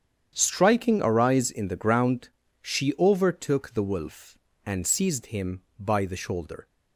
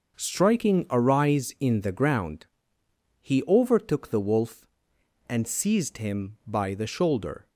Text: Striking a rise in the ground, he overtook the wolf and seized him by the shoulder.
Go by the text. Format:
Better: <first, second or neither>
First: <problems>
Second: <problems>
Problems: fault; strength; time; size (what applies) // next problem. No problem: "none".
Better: second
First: starts louder than the rest; strong; until 1.3 s; 8.5 dB // says "she" for "he"; at 2.5 s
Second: starts louder than the rest; noticeable; until 1.2 s; 6 dB